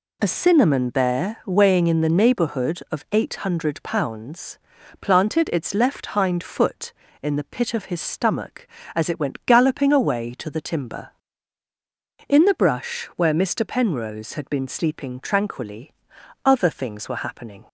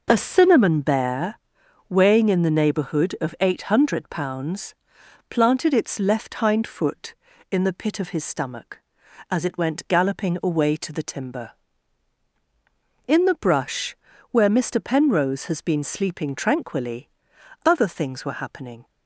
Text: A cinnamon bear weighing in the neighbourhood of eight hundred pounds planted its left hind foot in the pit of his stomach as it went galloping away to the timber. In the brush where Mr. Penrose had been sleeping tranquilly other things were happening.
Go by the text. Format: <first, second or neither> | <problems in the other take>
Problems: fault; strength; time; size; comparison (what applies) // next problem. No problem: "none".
first | pauses between "bear" and "weighing"; noticeable; at 1.3 s; 0.48 s long // pauses between "pounds" and "planted"; noticeable; at 4.7 s; 0.56 s long; also in the first // pauses between "brush" and "where"; slight; at 13.9 s; 0.36 s long // says "has" for "had"; at 15.4 s // pauses between "tranquilly" and "other"; noticeable; at 17.0 s; 0.58 s long; noticeable in the first